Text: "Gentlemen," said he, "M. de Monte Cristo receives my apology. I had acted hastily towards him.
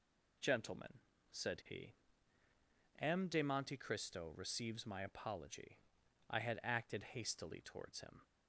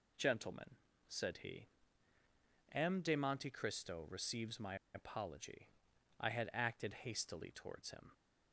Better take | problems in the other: first | pauses between "my" and "apology"; slight; at 4.7 s; 0.18 s long

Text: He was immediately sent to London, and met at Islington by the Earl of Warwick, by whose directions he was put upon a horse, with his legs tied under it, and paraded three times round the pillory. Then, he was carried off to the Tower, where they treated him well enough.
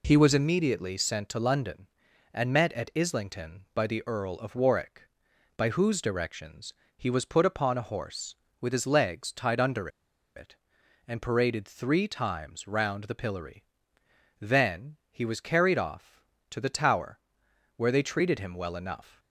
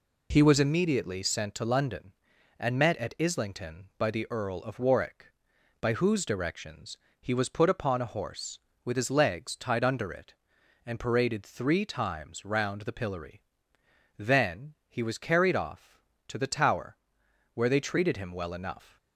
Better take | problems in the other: second | pauses between "directions" and "he"; slight; at 6.7 s; 0.22 s long; slight in the second // pauses between "under" and "it"; noticeable; at 9.8 s; 0.48 s long

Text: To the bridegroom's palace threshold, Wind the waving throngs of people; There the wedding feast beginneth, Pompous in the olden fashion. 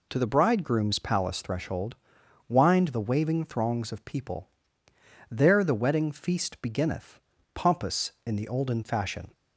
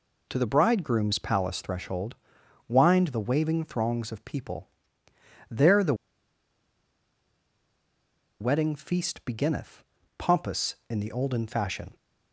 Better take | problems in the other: first | pauses between "the" and "wedding"; strong; at 5.9 s; 2.4 s long

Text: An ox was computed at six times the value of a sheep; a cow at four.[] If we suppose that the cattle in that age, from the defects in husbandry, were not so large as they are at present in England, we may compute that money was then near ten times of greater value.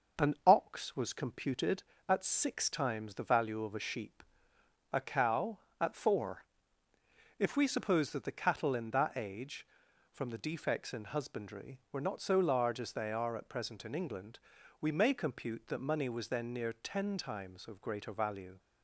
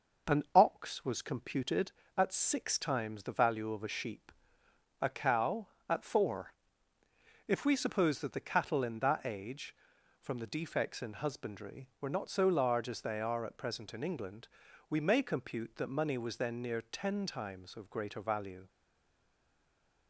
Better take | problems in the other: first | stays silent after the last word; noticeable; from 18.6 s on; 1.4 s long

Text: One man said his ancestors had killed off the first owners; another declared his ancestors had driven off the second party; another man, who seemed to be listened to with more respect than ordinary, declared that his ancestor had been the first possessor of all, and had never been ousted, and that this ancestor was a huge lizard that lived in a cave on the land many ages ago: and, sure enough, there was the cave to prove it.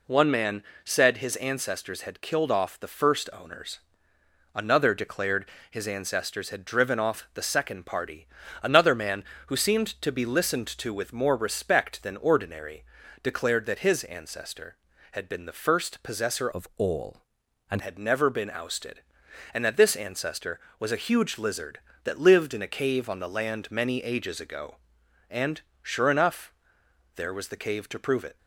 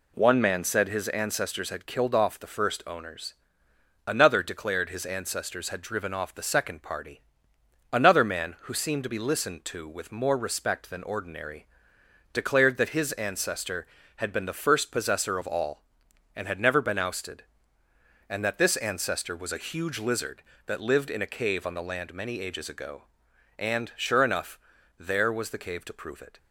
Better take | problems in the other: second | pauses between "man" and "said"; slight; at 0.6 s; 0.20 s long // pauses between "declared" and "his"; slight; at 5.4 s; 0.22 s long // changes voice from "of" to "and"; from 16.5 to 17.7 s; 1.2 s long

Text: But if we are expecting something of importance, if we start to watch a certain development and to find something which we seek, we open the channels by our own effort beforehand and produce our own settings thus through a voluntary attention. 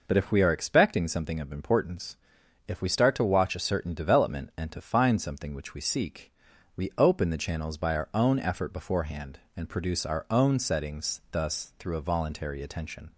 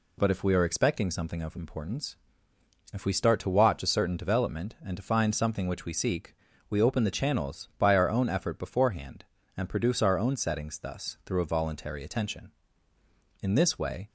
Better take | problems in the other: first | goes on to say "In this way"; noticeable; from 13.4 s on; 0.68 s long

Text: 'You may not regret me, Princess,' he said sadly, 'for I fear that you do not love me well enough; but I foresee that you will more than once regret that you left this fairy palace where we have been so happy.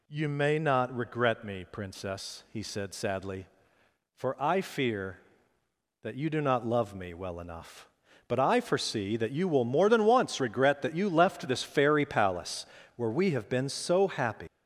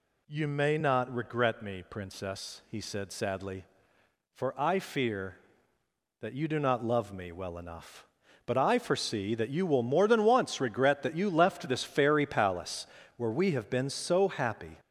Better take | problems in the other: second | pauses between "palace" and "where"; slight; at 12.6 s; 0.32 s long; slight in the second // leaves "happy" unfinished; at 14.4 s; 115 ms

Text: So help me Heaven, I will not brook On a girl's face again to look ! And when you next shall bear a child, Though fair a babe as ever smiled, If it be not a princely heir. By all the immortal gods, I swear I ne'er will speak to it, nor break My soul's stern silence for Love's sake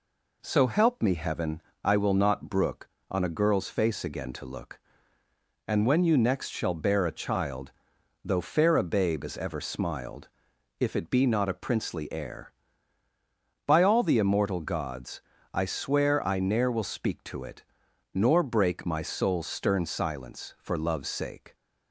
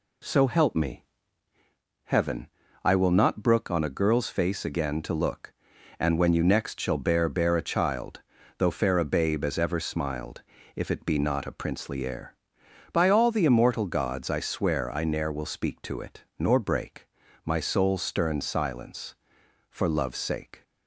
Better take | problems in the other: first | pauses between "me" and "Heaven"; at 1.0 s; 1.0 s long // says "bear" twice; at 7.2 s // pauses between "break" and "My"; at 17.0 s; 0.40 s long

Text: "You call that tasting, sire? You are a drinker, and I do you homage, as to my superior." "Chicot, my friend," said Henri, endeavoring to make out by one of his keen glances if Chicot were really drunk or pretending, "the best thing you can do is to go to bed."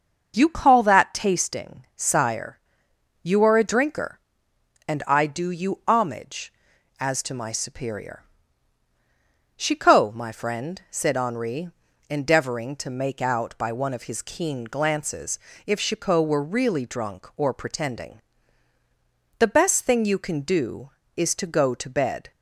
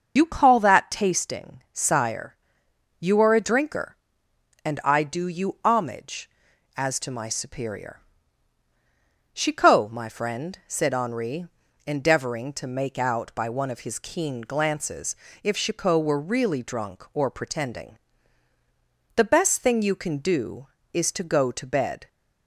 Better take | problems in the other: first | loses the start of "You"; at 0.1 s; 50 ms // starts louder than the rest; until 1.1 s; 6.5 dB; also in the first // pauses between "glances" and "if"; slight; at 15.1 s; 0.28 s long; slight in the first

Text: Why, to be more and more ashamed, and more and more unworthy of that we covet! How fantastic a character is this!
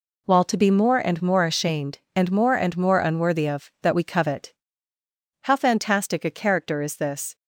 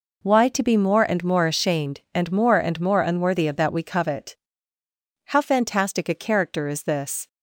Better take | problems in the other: second | says "While" for "Why"; at 0.2 s

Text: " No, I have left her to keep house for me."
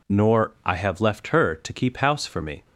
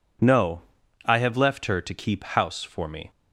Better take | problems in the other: second | says "Nor" for "No"; at 0.0 s

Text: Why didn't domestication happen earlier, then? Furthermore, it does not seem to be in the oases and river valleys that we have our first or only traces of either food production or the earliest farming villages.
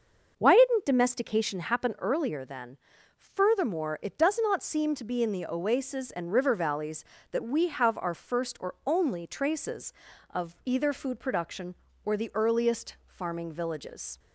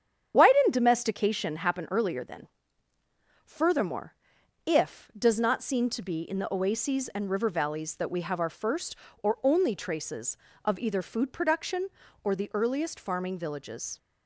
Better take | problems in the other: first | starts louder than the rest; strong; until 1.3 s; 9 dB; also in the first // says "if" for "it"; at 4.6 s

